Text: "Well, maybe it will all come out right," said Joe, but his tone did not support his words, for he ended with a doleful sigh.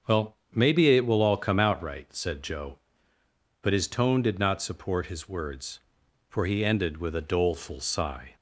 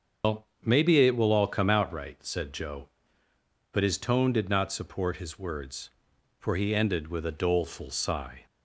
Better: first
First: starts louder than the rest; until 1.2 s; 6.5 dB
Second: loses the start of "Well"; at 0.2 s; 90 ms // starts louder than the rest; until 1.4 s; 6.5 dB

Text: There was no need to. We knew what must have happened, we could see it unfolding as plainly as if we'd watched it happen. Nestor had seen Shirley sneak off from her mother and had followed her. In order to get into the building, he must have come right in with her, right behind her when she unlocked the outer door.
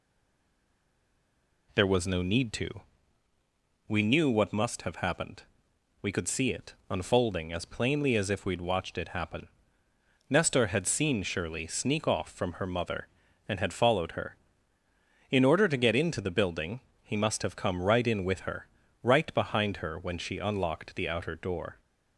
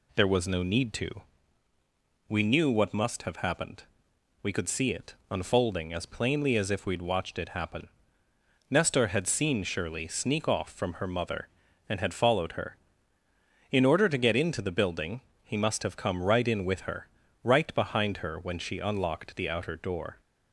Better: second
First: stays silent before the first word; noticeable; until 1.6 s; 1.6 s long // pauses between "it" and "unfolding"; slight; at 6.7 s; 0.16 s long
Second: pauses between "it" and "unfolding"; slight; at 5.1 s; 0.16 s long

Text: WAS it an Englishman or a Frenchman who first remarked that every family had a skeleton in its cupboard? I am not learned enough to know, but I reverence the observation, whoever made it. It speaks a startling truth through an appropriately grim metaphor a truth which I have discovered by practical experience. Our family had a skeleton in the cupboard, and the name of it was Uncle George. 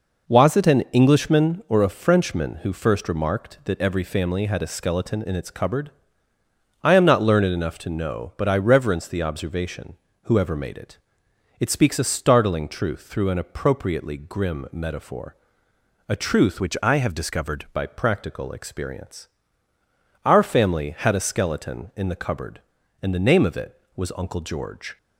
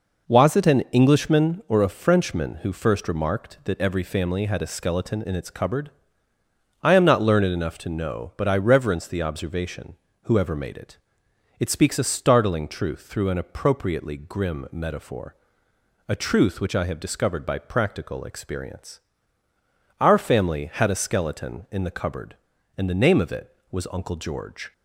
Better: second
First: pauses between "metaphor" and "a"; noticeable; at 15.3 s; 0.72 s long // changes voice from "which" to "discovered"; from 16.6 to 17.6 s; 1.0 s long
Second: pauses between "metaphor" and "a"; noticeable; at 15.3 s; 0.72 s long

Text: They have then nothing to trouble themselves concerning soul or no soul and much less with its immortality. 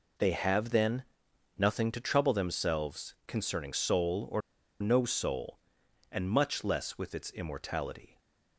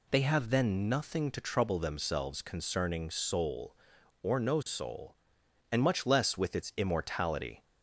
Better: second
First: pauses between "then" and "nothing"; noticeable; at 1.0 s; 0.54 s long // pauses between "or" and "no"; at 4.4 s; 0.39 s long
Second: none

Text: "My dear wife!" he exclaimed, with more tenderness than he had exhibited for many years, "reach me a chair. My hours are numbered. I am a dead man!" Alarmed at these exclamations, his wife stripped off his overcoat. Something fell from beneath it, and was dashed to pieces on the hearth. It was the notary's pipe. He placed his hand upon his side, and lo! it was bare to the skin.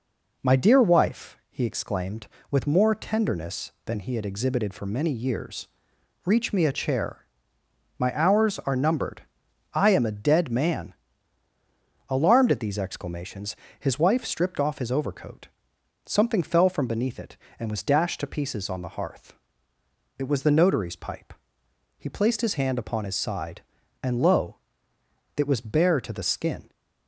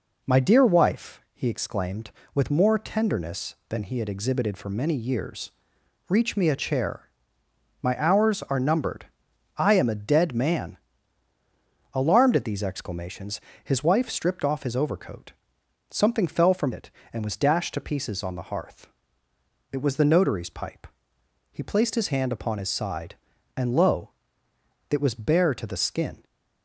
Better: first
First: none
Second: skips "beneath"; at 16.7 s

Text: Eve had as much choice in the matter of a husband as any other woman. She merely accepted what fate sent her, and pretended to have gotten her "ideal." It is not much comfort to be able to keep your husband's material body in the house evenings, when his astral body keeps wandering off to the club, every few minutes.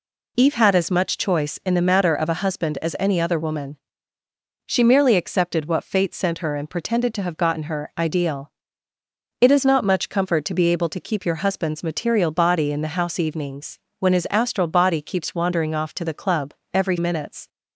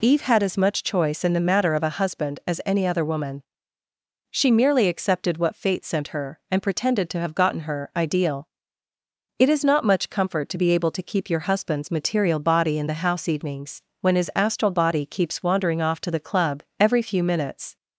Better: second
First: skips "few"; at 16.9 s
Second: none

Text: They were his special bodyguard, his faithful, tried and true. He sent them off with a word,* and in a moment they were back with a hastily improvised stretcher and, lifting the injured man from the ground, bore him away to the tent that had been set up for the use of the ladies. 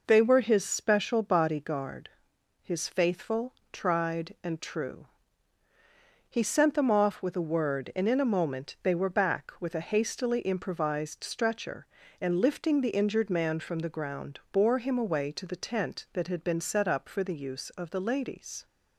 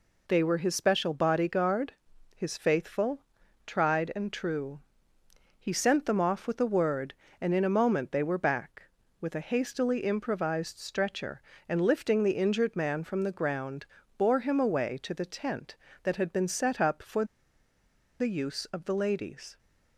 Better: first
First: none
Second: pauses between "for" and "the"; noticeable; at 17.2 s; 0.95 s long

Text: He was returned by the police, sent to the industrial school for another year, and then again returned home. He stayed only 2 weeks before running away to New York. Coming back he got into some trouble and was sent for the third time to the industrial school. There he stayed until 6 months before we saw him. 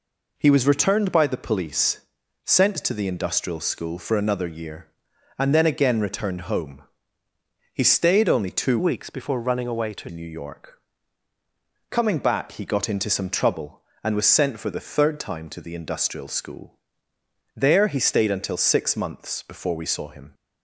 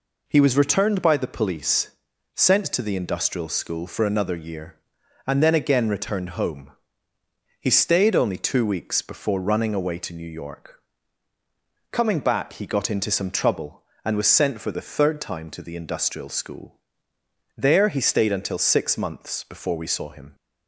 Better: second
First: changes voice from "weeks" to "to"; from 8.7 to 10.0 s; 1.3 s long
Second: none

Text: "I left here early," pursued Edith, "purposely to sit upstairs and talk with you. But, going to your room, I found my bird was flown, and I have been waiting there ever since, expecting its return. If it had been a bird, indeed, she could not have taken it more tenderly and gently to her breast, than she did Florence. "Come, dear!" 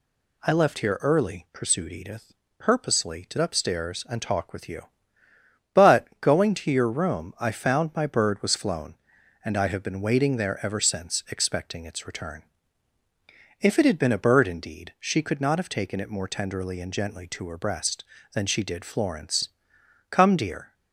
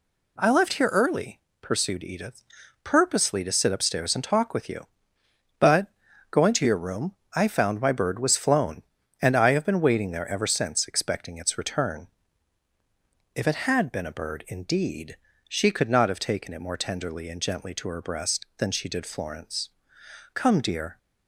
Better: second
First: skips "sit"; at 3.3 s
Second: none

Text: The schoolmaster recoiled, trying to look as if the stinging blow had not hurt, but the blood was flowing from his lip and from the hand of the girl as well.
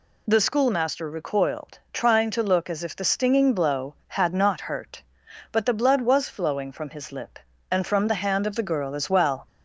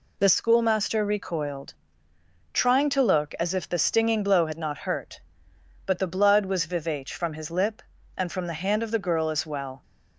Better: first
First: none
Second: says "vivace" for "flowing"; at 6.6 s

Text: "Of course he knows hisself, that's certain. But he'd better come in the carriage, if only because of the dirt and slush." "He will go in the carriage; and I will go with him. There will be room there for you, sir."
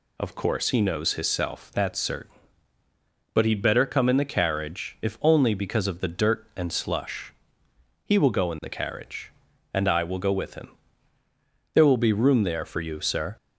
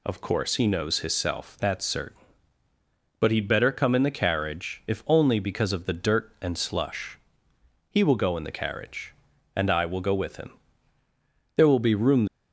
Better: first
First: none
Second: stops before "there for you sir"; at 12.2 s

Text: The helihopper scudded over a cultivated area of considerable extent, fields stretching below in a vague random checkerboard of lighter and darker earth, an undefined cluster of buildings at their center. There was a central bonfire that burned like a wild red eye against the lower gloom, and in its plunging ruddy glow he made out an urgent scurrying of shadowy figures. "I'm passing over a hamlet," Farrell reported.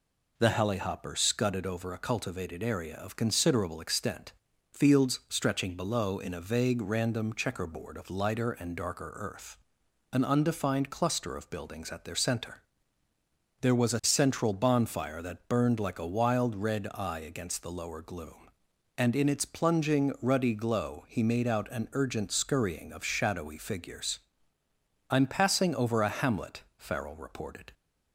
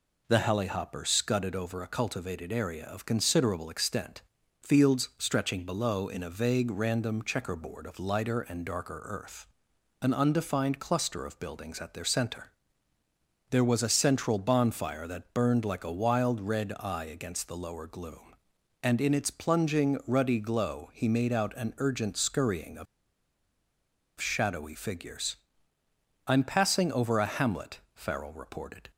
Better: first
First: none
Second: pauses between "of" and "shadowy"; strong; at 22.8 s; 1.3 s long

